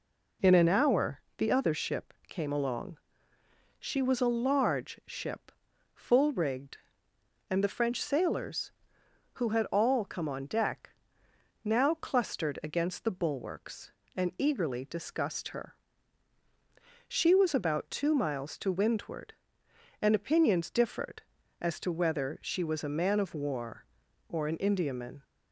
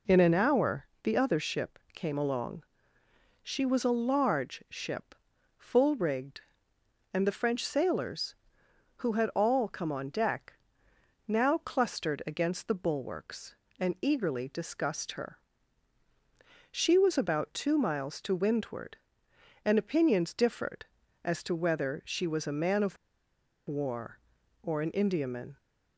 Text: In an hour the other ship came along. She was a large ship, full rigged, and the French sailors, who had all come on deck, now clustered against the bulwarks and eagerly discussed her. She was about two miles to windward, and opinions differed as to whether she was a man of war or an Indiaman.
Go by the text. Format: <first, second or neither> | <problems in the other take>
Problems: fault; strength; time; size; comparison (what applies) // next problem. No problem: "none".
first | pauses between "hour" and "the"; slight; at 0.8 s; 0.16 s long; slight in the first // pauses between "of" and "war"; noticeable; at 22.9 s; 0.71 s long